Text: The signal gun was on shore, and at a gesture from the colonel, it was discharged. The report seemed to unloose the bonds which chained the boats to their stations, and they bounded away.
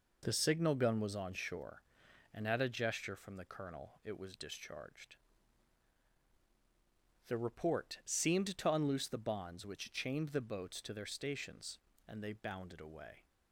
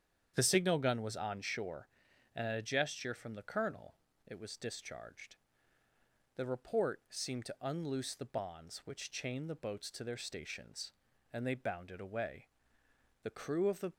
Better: first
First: none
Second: starts louder than the rest; strong; until 1.3 s; 8.5 dB // goes on to say "The crew of the"; noticeable; from 13.2 s on; 0.70 s long

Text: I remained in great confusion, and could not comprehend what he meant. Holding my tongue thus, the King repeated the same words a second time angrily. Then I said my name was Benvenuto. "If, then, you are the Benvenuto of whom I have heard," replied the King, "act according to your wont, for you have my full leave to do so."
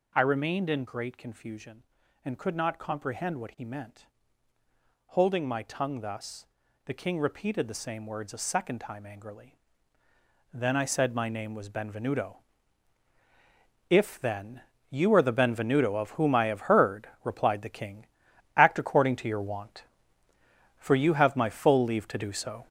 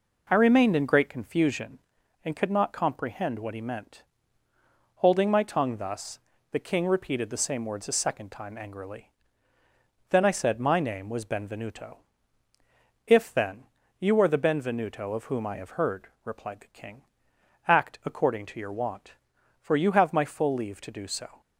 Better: second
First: gets louder; throughout; 6 dB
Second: none

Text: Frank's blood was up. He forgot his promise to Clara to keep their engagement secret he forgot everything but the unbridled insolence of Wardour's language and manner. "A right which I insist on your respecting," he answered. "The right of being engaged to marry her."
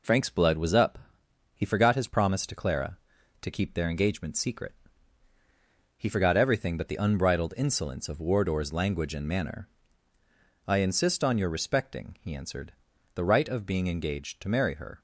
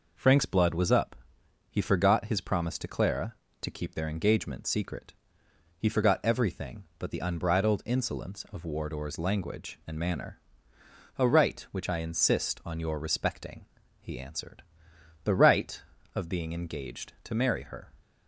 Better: second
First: pauses between "secret" and "he"; at 4.7 s; 1.2 s long // skips "A right which"; at 10.1 s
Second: pauses between "secret" and "he"; noticeable; at 5.1 s; 0.66 s long

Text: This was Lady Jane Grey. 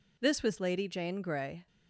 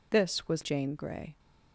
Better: first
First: none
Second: skips "Lady"; at 0.6 s

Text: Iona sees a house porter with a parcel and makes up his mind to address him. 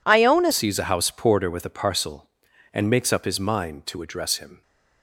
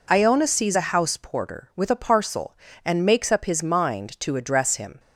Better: second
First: changes voice at "sees"; from 0.5 s on; 4.1 s long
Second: none

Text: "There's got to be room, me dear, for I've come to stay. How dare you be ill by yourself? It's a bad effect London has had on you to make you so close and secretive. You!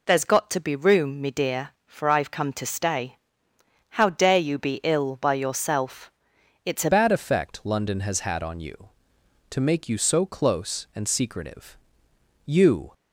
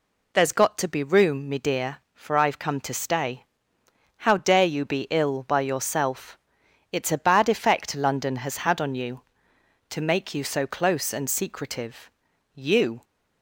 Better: second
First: changes voice at "bad"; from 6.9 s on; 6.0 s long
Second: none

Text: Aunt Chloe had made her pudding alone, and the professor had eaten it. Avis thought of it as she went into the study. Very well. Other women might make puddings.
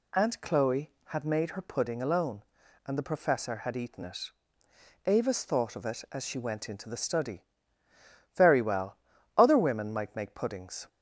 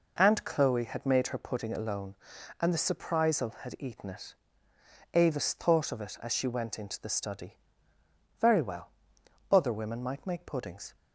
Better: first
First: none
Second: says "surprisal" for "professor"; at 2.7 s

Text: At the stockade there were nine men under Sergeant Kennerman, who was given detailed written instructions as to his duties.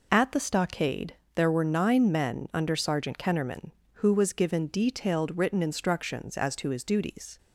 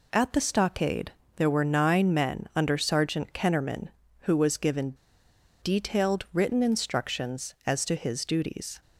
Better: first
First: pauses between "stockade" and "there"; slight; at 1.1 s; 0.18 s long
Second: pauses between "stockade" and "there"; slight; at 1.1 s; 0.24 s long // pauses between "given" and "detailed"; noticeable; at 4.9 s; 0.68 s long

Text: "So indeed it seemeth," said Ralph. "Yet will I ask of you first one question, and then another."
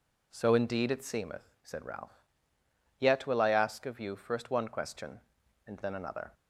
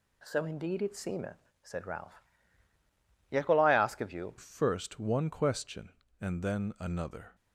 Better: first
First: none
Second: changes voice at "first"; from 4.3 s on; 3.0 s long

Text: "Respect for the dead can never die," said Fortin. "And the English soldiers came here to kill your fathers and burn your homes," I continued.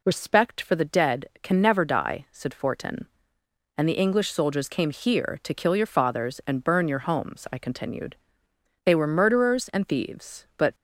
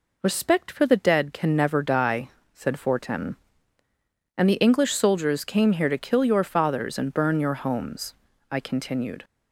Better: second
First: goes on to say "They were murderers and thieves but"; strong; from 8.8 s on; 1.9 s long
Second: none

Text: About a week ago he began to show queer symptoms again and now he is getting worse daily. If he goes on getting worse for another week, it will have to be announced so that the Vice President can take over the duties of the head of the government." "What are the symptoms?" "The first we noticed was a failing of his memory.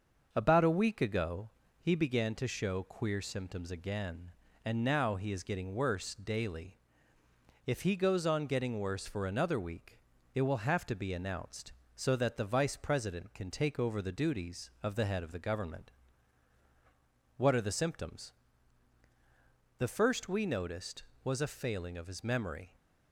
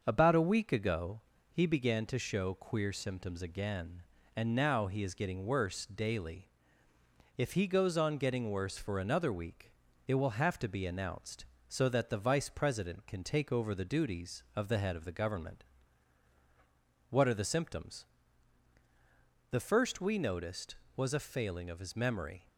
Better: neither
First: starts louder than the rest; until 1.3 s; 6.5 dB // pauses between "ago" and "he"; slight; at 1.5 s; 0.30 s long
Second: starts louder than the rest; until 1.0 s; 6.5 dB // pauses between "ago" and "he"; slight; at 1.2 s; 0.30 s long

